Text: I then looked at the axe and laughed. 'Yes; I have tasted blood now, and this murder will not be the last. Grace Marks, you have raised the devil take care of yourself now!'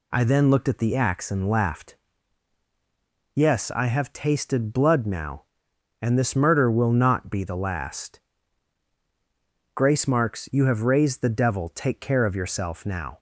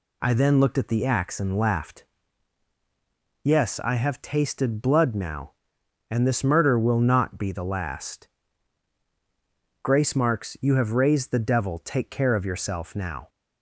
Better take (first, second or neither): neither